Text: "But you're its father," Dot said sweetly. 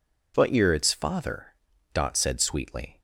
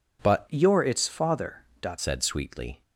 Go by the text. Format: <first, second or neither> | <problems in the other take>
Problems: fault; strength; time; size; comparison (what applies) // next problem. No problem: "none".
first | changes voice from "you're" to "Dot"; from 0.4 to 1.9 s; 1.5 s long